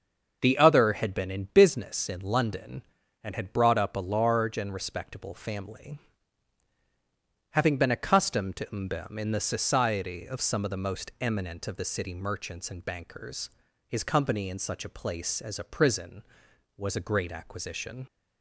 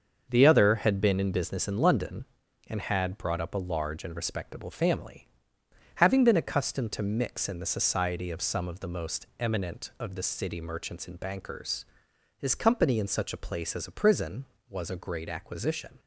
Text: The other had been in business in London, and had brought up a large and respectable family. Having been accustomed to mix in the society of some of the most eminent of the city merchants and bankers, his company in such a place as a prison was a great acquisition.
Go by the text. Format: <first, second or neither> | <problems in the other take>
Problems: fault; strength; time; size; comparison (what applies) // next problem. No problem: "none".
second | starts louder than the rest; until 1.4 s; 6.5 dB; also in the second // says "mbem" for "mix"; at 8.6 s